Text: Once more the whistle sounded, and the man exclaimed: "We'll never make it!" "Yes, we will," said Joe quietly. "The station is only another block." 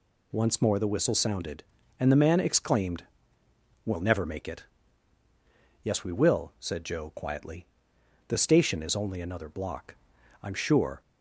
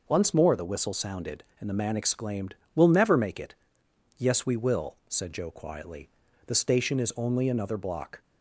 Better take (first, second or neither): second